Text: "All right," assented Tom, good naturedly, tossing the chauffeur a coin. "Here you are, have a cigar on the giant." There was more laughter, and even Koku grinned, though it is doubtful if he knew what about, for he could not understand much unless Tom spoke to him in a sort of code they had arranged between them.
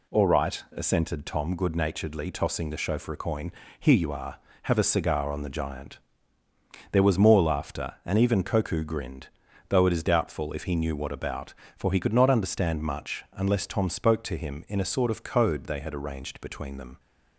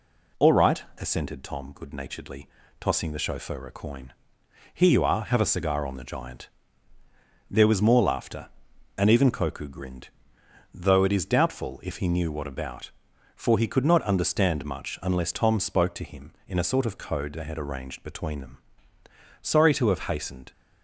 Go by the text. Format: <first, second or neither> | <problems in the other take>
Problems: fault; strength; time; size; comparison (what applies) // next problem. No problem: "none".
first | goes on to say "Sorry to have hastened"; noticeable; from 19.4 s on; 1.1 s long